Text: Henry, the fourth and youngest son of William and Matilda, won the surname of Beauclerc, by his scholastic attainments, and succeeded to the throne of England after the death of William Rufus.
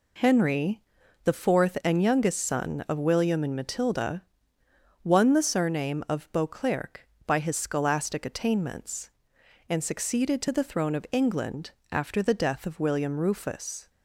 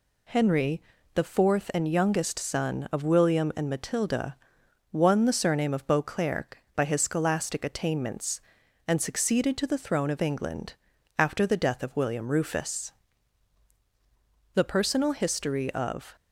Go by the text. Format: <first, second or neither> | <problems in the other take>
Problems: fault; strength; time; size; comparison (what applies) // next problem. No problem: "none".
first | pauses between "England" and "after"; at 10.7 s; 0.42 s long; slight in the first // goes on to say "The personal history of"; from 14.5 s on; 1.6 s long